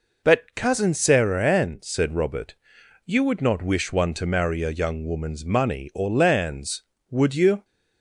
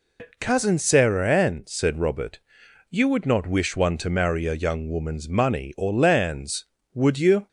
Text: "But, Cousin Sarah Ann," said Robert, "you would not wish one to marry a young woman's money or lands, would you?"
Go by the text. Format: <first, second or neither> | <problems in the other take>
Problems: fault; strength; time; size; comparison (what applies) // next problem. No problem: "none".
first | loses the start of "But"; at 0.1 s; 110 ms